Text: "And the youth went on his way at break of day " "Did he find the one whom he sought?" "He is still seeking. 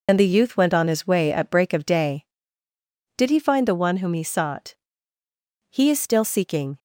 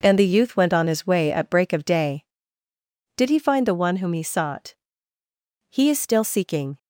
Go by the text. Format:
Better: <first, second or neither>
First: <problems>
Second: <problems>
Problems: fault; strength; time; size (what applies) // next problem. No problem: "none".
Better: second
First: loses the start of "And"; at 0.0 s; 75 ms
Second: none